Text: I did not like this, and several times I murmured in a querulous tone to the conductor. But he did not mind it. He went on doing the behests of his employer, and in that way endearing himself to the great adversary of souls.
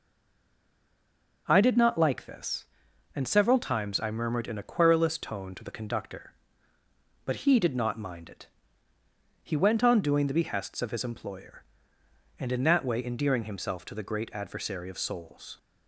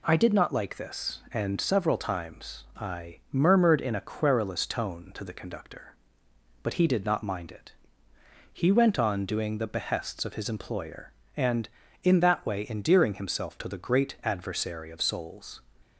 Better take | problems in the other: second | stays silent before the first word; noticeable; until 1.4 s; 1.4 s long

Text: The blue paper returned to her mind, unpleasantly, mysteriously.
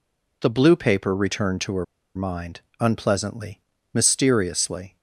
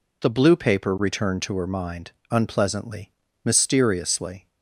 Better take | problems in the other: second | pauses between "her" and "mind"; slight; at 1.8 s; 0.30 s long

